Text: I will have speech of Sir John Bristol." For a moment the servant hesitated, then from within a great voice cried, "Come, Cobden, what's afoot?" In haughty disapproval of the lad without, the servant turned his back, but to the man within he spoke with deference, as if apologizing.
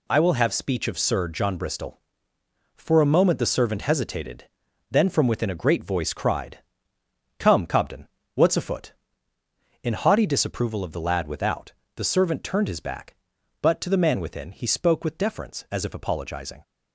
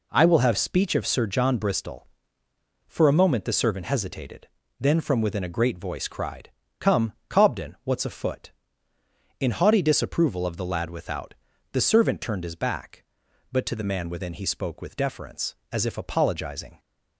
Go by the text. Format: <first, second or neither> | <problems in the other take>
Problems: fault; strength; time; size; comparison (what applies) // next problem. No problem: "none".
neither | none